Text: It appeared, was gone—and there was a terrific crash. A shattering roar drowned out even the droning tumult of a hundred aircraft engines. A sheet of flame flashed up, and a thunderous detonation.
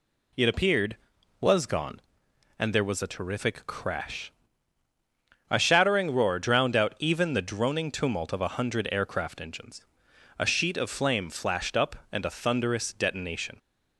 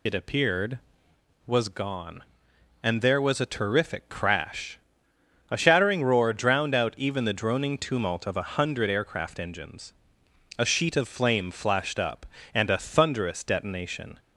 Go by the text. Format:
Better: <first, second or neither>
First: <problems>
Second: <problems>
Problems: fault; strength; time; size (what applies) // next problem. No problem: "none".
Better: first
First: none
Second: loses the start of "It"; at 0.0 s; 65 ms